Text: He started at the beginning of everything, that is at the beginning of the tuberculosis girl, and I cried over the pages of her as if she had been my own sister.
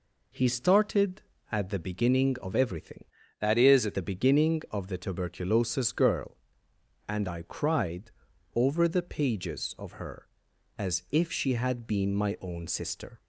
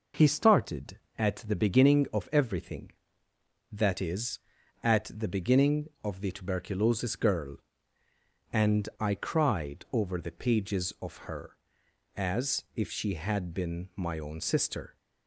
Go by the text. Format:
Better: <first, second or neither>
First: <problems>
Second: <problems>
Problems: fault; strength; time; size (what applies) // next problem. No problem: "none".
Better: second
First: changes voice from "that" to "at"; from 3.3 to 3.9 s; 0.6 s long // pauses between "cried" and "over"; at 8.1 s; 0.42 s long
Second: none